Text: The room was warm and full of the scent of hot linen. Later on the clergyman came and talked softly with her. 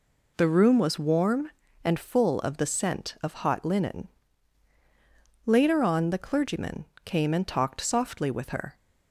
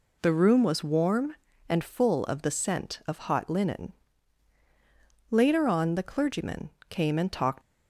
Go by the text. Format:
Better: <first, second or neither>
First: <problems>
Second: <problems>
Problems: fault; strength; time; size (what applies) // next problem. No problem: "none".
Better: first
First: pauses between "clergyman" and "came"; slight; at 6.8 s; 0.18 s long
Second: pauses between "clergyman" and "came"; slight; at 6.7 s; 0.18 s long // stops before "softly with her"; at 7.6 s